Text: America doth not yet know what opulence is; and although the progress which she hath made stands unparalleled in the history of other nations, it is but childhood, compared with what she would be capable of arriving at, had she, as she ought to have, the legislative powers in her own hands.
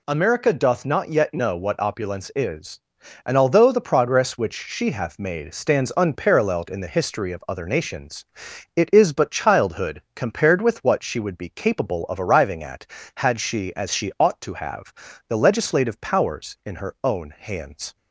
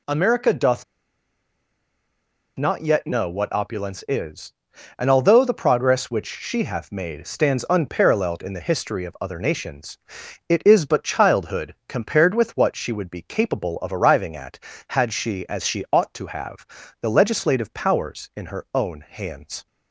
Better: first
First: none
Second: pauses between "doth" and "not"; strong; at 0.8 s; 1.7 s long

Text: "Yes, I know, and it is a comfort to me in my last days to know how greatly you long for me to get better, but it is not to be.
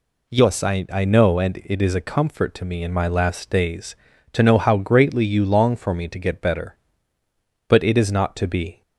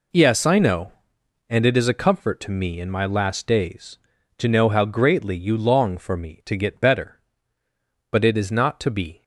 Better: second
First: says "I" twice; at 0.9 s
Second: none

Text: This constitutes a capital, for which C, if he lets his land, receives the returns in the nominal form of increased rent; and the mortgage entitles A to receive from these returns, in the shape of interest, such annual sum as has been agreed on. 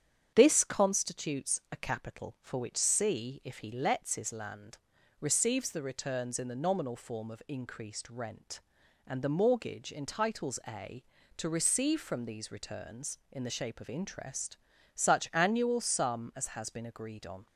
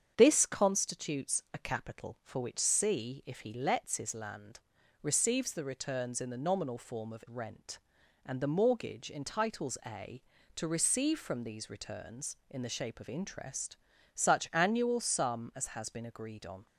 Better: first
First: starts louder than the rest; strong; until 1.3 s; 8.5 dB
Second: starts louder than the rest; strong; until 1.1 s; 8 dB // skips "increased"; at 7.2 s

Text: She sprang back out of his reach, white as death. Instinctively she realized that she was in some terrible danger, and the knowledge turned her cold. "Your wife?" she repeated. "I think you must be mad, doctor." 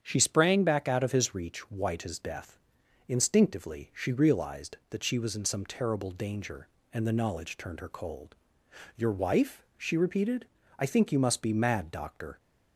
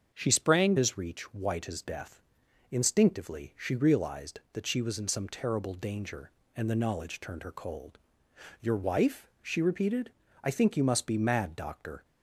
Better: first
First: starts louder than the rest; strong; until 1.0 s; 8 dB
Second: starts louder than the rest; until 1.1 s; 7 dB // skips "back out of"; at 0.7 s

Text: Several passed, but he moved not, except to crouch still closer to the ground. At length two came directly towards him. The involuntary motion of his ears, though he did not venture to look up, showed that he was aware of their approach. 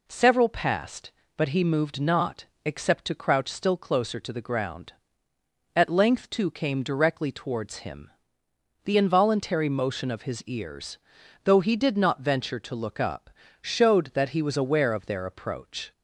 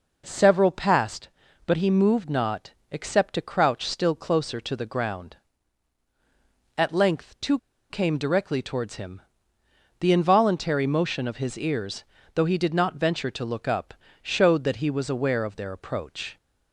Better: first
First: none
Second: pauses between "two" and "came"; slight; at 7.5 s; 0.31 s long

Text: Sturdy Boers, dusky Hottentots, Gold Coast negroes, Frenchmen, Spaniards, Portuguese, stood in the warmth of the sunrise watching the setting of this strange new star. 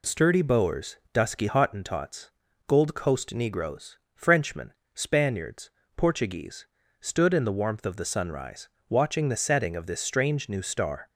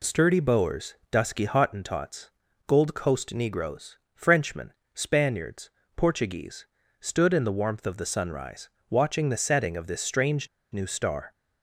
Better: first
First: pauses between "sunrise" and "watching"; slight; at 8.6 s; 0.20 s long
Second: pauses between "sunrise" and "watching"; slight; at 8.6 s; 0.20 s long // pauses between "strange" and "new"; slight; at 10.4 s; 0.24 s long

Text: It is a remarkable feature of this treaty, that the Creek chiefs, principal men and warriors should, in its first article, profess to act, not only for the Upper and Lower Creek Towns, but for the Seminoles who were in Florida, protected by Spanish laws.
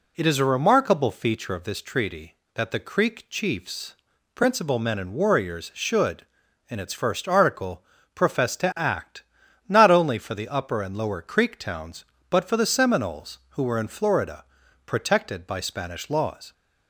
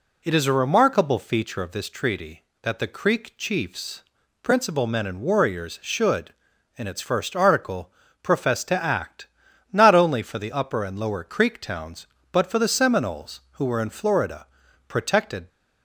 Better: first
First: none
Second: stops before "by Spanish laws"; at 15.4 s

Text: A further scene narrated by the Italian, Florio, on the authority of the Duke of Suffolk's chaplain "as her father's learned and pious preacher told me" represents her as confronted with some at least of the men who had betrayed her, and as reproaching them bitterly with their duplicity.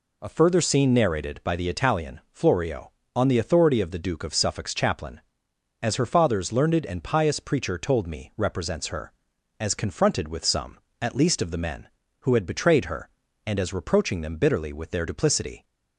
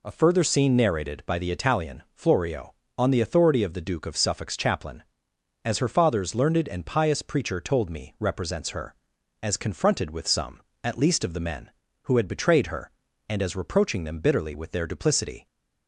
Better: neither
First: none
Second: none

